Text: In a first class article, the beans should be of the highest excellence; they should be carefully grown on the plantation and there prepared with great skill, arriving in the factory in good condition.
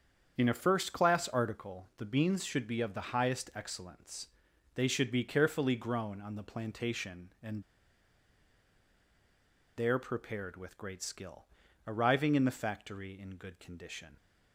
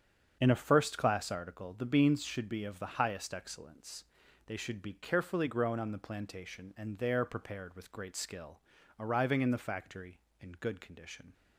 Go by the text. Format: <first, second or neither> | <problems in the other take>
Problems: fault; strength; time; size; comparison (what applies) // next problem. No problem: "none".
second | starts louder than the rest; strong; until 1.3 s; 7.5 dB; strong in the second // pauses between "and" and "there"; strong; at 7.6 s; 2.1 s long